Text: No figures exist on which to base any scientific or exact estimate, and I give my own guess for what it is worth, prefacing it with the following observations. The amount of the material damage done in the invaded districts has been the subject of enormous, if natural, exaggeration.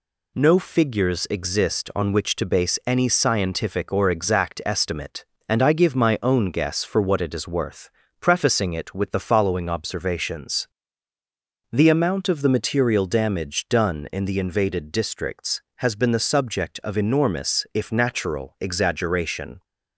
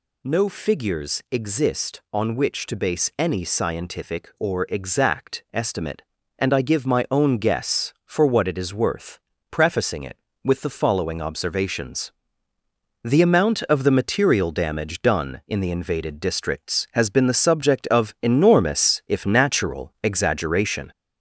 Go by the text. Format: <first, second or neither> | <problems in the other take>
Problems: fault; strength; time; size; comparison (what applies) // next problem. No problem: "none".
first | gets louder; throughout; 3.5 dB